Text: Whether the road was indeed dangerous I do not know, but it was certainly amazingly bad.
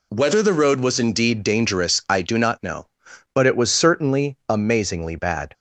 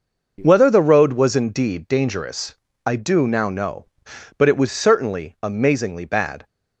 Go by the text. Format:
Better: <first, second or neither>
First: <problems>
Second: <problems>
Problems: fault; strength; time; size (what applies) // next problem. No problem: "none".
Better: first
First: none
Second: pauses between "dangerous" and "I"; slight; at 2.5 s; 0.30 s long // says "now" for "not"; at 3.2 s